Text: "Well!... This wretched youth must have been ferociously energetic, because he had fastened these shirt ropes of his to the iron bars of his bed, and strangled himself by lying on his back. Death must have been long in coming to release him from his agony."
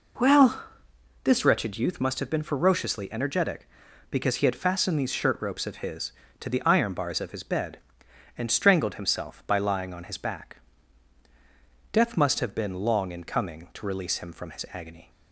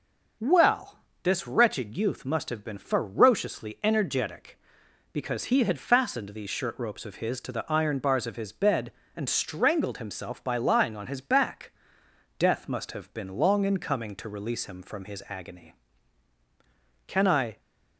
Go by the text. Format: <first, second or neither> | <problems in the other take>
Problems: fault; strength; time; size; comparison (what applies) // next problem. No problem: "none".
first | starts louder than the rest; noticeable; until 1.6 s; 6 dB // goes on to say "Can I"; from 17.0 s on; 0.52 s long